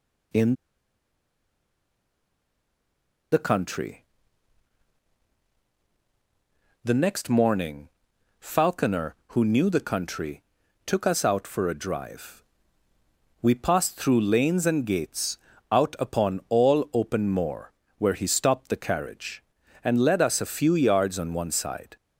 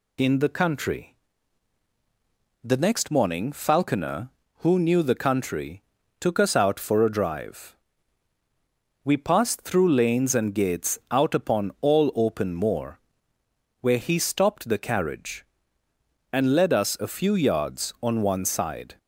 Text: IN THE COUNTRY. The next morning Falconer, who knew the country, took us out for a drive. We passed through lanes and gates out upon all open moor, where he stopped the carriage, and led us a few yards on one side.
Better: second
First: pauses between "IN" and "THE"; strong; at 0.5 s; 2.7 s long // pauses between "morning" and "Falconer"; noticeable; at 7.8 s; 0.50 s long // pauses between "gates" and "out"; slight; at 15.3 s; 0.34 s long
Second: none

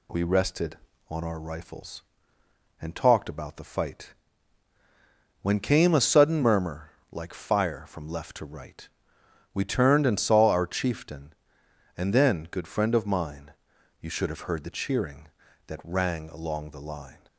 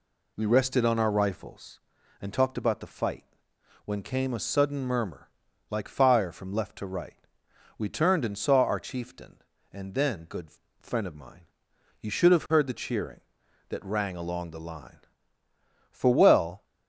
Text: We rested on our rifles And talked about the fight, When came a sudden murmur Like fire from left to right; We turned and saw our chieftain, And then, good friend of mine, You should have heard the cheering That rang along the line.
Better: first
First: pauses between "murmur" and "Like"; slight; at 6.9 s; 0.20 s long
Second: pauses between "murmur" and "Like"; at 5.2 s; 0.40 s long // pauses between "good" and "friend"; slight; at 10.4 s; 0.32 s long // goes on to say "For well"; noticeable; from 15.8 s on; 0.74 s long

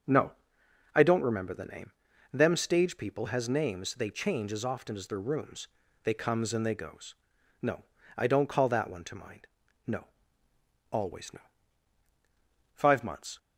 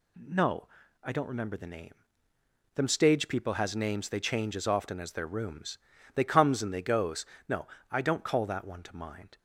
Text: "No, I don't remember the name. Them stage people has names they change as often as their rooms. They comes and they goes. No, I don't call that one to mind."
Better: second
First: starts louder than the rest; until 1.7 s; 6.5 dB // goes on to say "No Always no Five months"; strong; from 9.8 s on; 3.5 s long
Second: none

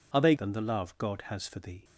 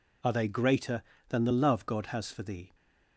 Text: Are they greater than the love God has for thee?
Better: second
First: skips "greater"; at 0.3 s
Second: none

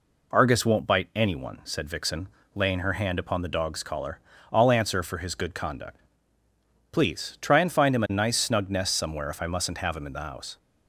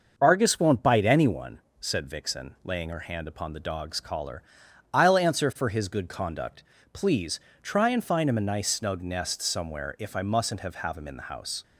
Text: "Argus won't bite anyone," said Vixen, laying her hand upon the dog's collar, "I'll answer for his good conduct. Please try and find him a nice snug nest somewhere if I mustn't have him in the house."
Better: first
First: none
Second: starts louder than the rest; noticeable; until 1.1 s; 6 dB // pauses between "Please" and "try"; slight; at 7.3 s; 0.24 s long // says "have" twice; at 10.7 s

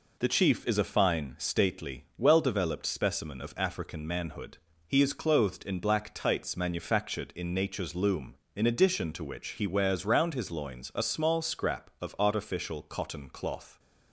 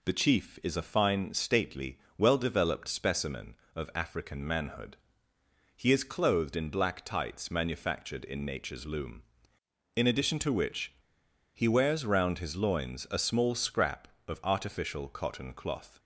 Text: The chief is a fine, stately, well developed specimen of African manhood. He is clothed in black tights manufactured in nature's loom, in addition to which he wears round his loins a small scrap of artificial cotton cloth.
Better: first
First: none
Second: pauses between "which" and "he"; noticeable; at 10.9 s; 0.63 s long

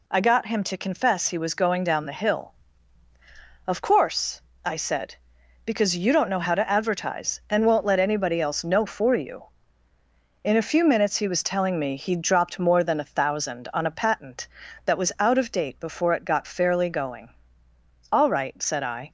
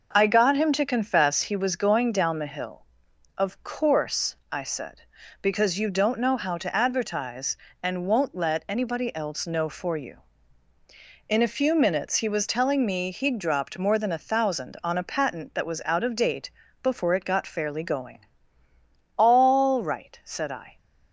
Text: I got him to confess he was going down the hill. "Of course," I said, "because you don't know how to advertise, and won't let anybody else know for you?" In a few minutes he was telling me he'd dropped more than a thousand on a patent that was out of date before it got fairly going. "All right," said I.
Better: first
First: none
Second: starts louder than the rest; noticeable; until 1.4 s; 5.5 dB // pauses between "date" and "before"; slight; at 16.4 s; 0.32 s long

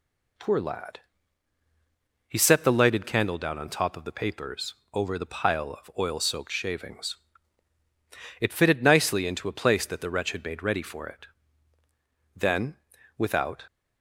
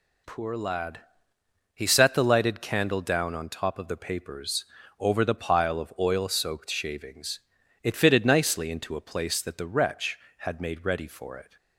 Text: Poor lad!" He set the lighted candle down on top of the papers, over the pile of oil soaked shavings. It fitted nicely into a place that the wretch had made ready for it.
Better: second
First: goes on to say "Then without"; noticeable; from 12.3 s on; 1.3 s long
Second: none

